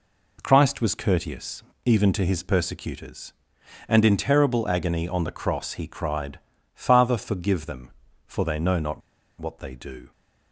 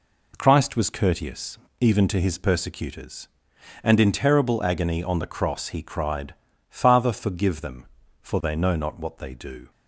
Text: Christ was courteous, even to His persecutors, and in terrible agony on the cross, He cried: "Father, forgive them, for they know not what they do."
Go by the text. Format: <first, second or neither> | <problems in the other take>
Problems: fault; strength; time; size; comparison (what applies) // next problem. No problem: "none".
second | pauses between "not" and "what"; at 9.0 s; 0.40 s long